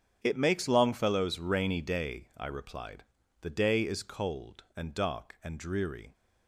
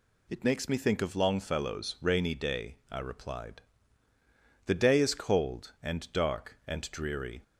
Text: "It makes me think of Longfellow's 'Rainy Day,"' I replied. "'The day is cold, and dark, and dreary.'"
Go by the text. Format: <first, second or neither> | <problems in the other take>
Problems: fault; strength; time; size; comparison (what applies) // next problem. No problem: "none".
second | starts louder than the rest; strong; until 1.2 s; 8 dB // skips "me think of"; at 0.6 s